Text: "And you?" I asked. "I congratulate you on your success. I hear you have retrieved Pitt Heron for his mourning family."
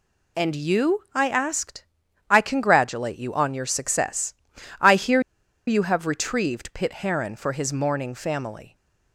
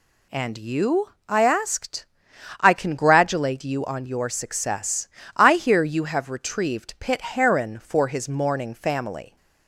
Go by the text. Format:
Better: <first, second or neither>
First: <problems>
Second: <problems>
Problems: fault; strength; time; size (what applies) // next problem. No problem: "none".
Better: second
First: pauses between "hear" and "you"; noticeable; at 5.2 s; 0.46 s long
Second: none